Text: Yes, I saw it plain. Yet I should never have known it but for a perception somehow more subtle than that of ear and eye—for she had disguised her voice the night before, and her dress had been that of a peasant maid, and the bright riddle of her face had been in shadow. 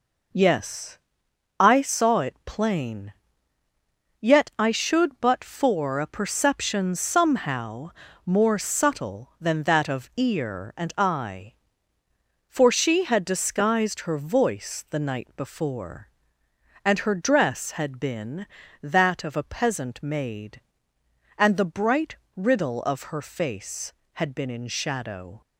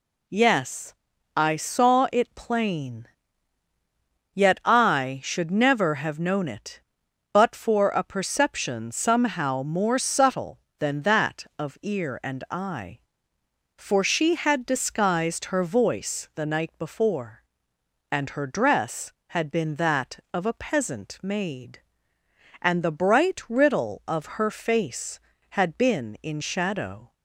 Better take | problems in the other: second | skips "never have known it"; at 5.1 s // pauses between "somehow" and "more"; slight; at 7.8 s; 0.34 s long // pauses between "bright" and "riddle"; slight; at 22.1 s; 0.22 s long

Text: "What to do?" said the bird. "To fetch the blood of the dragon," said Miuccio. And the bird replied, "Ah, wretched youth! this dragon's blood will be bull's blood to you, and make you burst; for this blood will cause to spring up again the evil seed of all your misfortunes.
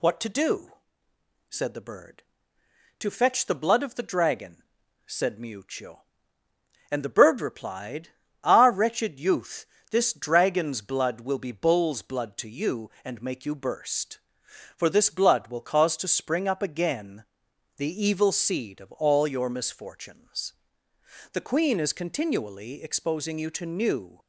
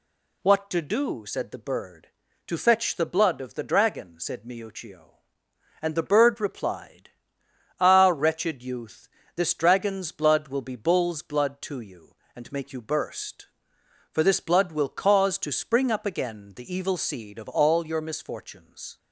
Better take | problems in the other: second | pauses between "again" and "the"; noticeable; at 17.2 s; 0.52 s long // goes on to say "The Queen is continually exposing you to new"; strong; from 21.3 s on; 2.8 s long

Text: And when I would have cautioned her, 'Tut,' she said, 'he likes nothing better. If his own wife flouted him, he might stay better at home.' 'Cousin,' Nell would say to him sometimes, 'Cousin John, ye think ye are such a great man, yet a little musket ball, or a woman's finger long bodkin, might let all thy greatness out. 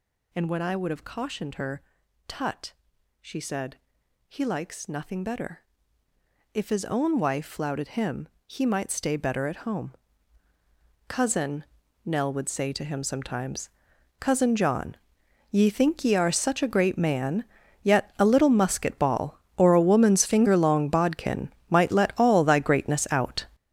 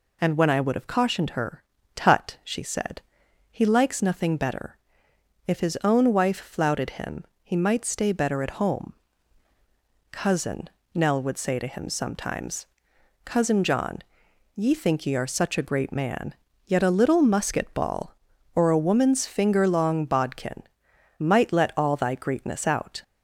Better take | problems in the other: second | gets louder; strong; throughout; 11 dB

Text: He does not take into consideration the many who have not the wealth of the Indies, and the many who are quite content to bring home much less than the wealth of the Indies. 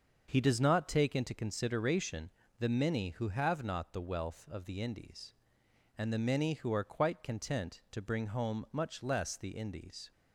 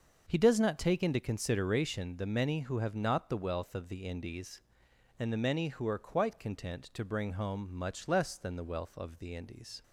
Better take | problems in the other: second | starts louder than the rest; until 1.2 s; 6.5 dB; also in the second // pauses between "consideration" and "the"; slight; at 2.2 s; 0.30 s long // skips "than the wealth of"; at 9.3 s

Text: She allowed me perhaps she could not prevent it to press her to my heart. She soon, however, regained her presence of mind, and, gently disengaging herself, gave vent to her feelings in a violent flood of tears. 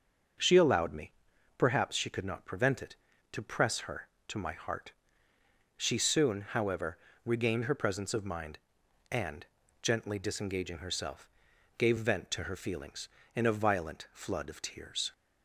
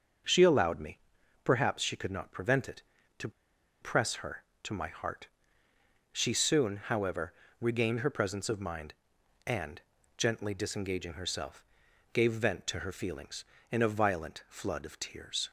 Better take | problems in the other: first | starts louder than the rest; until 1.7 s; 6.5 dB; also in the first // pauses between "me" and "perhaps"; noticeable; at 0.9 s; 0.46 s long; noticeable in the first // pauses between "to" and "press"; noticeable; at 3.2 s; 0.51 s long

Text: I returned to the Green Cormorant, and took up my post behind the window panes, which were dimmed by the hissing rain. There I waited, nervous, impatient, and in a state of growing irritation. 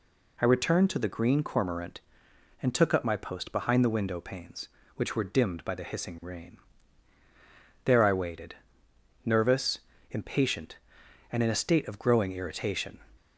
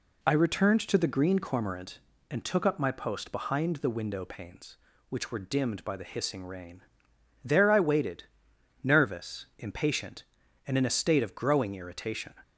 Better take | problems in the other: neither | none

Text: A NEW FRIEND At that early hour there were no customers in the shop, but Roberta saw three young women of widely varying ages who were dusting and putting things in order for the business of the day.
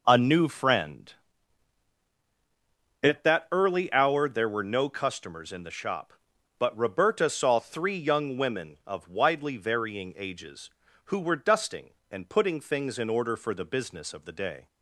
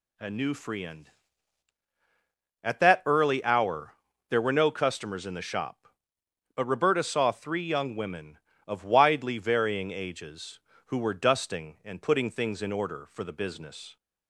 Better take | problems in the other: first | pauses between "hour" and "there"; at 3.9 s; 0.38 s long // stops before "of the day"; at 13.9 s

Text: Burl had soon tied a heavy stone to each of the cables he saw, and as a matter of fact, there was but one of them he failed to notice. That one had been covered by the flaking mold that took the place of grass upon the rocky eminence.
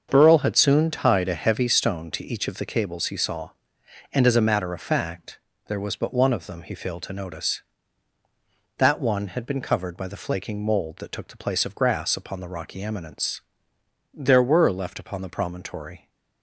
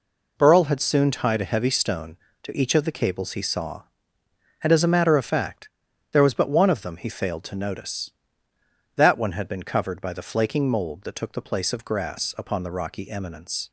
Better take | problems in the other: second | starts louder than the rest; until 1.1 s; 6.5 dB // goes on to say "There were left upon the promontory"; strong; from 14.1 s on; 1.9 s long

